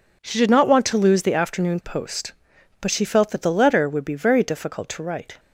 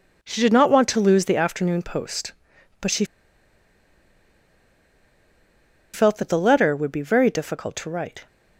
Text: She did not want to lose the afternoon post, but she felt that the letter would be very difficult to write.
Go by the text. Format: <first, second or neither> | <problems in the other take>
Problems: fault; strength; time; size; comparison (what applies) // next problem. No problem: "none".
first | pauses between "she" and "felt"; strong; at 3.0 s; 2.8 s long